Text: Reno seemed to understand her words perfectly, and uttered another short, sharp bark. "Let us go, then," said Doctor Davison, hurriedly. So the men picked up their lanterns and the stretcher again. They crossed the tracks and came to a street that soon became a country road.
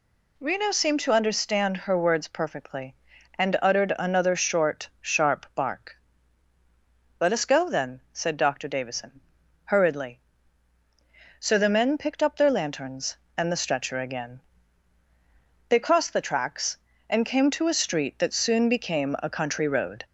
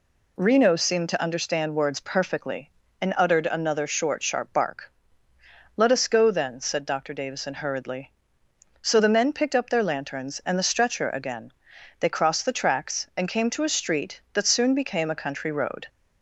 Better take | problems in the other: first | skips "her"; at 1.7 s

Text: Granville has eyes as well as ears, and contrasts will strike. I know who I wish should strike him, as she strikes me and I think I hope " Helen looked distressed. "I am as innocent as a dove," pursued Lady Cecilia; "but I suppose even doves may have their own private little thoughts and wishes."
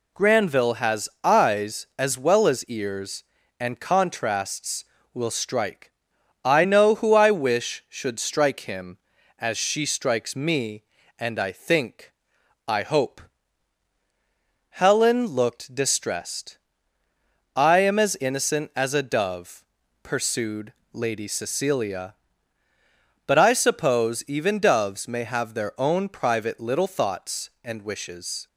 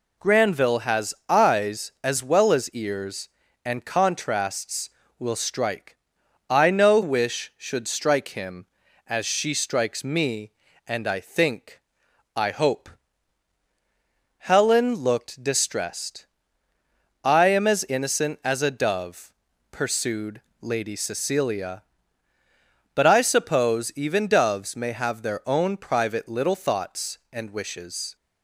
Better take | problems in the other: first | skips "who I"; at 7.0 s // pauses between "think" and "I"; noticeable; at 11.7 s; 0.56 s long; noticeable in the first // pauses between "pursued" and "Lady"; slight; at 20.4 s; 0.20 s long; slight in the first

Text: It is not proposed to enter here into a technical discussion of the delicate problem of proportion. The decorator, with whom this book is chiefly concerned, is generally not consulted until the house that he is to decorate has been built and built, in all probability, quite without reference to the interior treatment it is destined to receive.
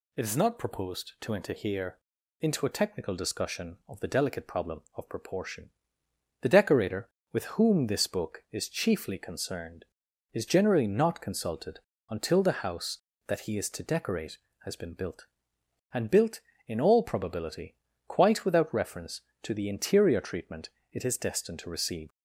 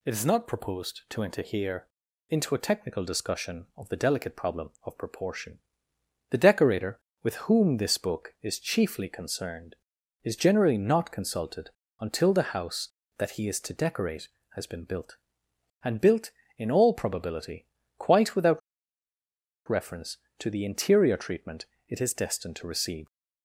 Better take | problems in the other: first | pauses between "here" and "into"; at 1.8 s; 0.44 s long; also in the first // pauses between "consulted" and "until"; slight; at 11.6 s; 0.30 s long; slight in the first // pauses between "without" and "reference"; at 18.6 s; 1.0 s long // pauses between "treatment" and "it"; slight; at 21.6 s; 0.24 s long; slight in the first

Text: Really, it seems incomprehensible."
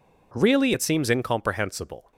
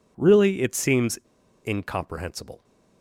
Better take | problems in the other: first | pauses between "seems" and "incomprehensible"; noticeable; at 1.1 s; 0.46 s long

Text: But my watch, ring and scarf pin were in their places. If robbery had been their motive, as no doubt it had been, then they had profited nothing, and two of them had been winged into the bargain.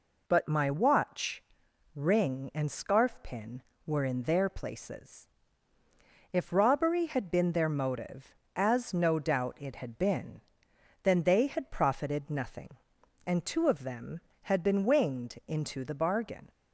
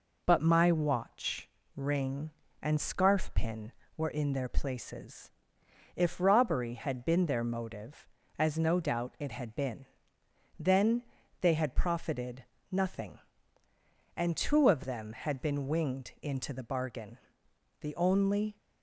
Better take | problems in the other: first | pauses between "then" and "they"; at 11.0 s; 0.38 s long // pauses between "profited" and "nothing"; slight; at 12.4 s; 0.26 s long // goes on to say "The only"; noticeable; from 17.8 s on; 0.76 s long

